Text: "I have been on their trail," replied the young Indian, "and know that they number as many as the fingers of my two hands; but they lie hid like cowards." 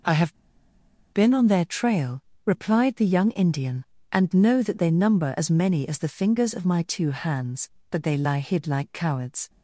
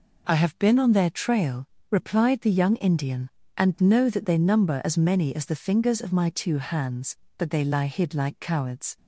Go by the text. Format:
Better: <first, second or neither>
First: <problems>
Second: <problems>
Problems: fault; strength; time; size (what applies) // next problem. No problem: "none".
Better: second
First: pauses between "have" and "been"; noticeable; at 0.3 s; 0.78 s long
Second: none